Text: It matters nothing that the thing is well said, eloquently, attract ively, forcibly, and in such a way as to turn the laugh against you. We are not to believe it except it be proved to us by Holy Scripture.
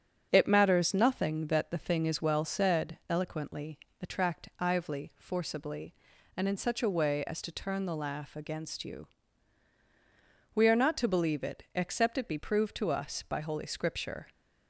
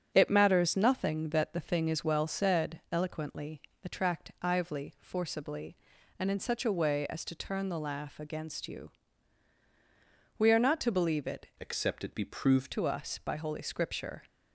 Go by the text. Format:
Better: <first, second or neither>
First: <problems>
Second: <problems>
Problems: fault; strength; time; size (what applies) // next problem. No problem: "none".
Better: first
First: starts louder than the rest; strong; until 1.3 s; 7.5 dB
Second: starts louder than the rest; strong; until 1.1 s; 8 dB // changes voice from "except" to "proved"; from 11.5 to 12.7 s; 1.2 s long